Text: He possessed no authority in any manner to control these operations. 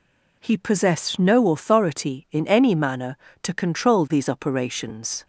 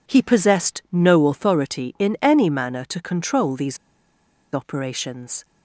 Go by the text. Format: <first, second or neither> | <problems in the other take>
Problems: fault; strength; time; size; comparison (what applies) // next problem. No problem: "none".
first | pauses between "these" and "operations"; noticeable; at 3.7 s; 0.76 s long